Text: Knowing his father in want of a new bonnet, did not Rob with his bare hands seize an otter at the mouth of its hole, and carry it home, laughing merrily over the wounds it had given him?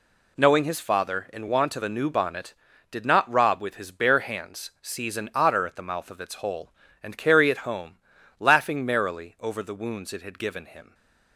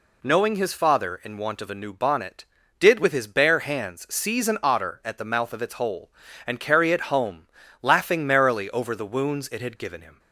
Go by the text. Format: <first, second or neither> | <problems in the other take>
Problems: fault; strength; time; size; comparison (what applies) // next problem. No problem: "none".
first | skips "not Rob"; at 2.9 s